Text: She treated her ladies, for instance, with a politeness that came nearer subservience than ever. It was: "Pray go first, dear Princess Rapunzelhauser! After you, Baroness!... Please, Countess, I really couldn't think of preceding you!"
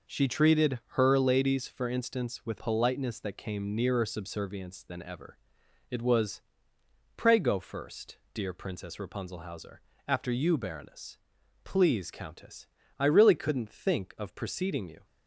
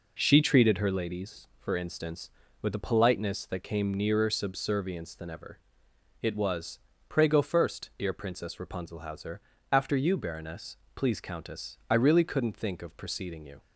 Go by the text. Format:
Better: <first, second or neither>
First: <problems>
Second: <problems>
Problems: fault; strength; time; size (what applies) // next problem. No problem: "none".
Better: second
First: skips "a"; at 2.5 s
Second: none